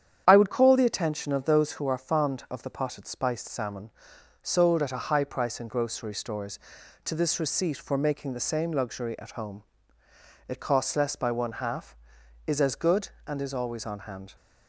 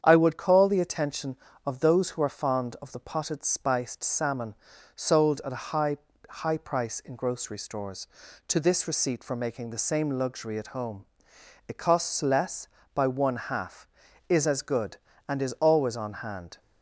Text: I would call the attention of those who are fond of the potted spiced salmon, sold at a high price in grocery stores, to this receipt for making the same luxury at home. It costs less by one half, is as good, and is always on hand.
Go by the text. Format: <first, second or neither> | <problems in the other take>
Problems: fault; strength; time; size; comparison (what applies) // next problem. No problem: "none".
first | starts louder than the rest; strong; until 1.0 s; 8 dB; strong in the first // says "high" twice; at 6.2 s